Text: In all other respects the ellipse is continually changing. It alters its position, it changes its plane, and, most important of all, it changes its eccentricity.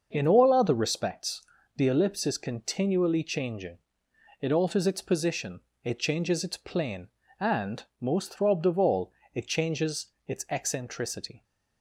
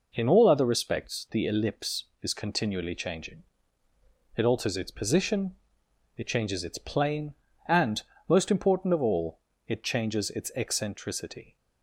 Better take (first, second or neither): second